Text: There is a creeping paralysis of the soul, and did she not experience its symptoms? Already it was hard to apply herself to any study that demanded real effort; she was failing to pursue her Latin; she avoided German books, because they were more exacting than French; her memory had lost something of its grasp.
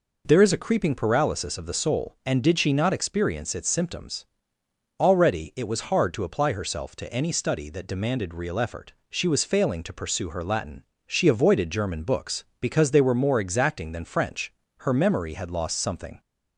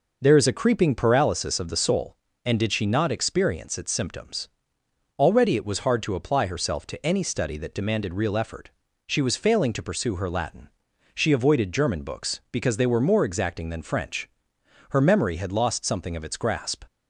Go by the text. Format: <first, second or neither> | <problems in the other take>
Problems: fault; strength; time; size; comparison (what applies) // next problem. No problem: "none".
second | stops before "of its grasp"; at 16.1 s